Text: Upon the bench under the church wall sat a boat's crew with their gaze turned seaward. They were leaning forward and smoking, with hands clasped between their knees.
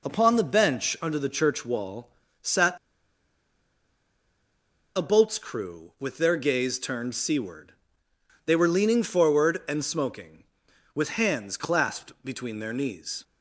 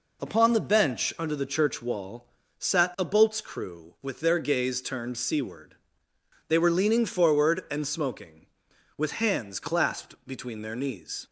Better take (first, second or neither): second